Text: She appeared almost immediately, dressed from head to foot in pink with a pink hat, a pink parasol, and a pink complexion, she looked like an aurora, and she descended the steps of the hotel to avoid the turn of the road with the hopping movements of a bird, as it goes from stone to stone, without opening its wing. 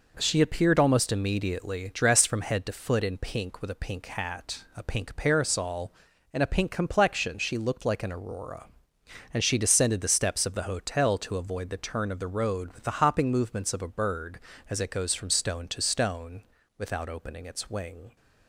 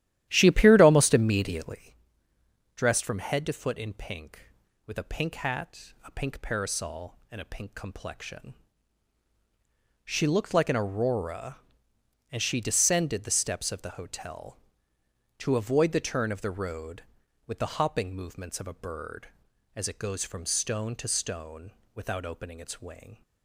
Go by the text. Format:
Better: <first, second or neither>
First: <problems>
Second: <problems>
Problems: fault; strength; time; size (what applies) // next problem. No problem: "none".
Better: first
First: none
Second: starts louder than the rest; strong; until 1.8 s; 12.5 dB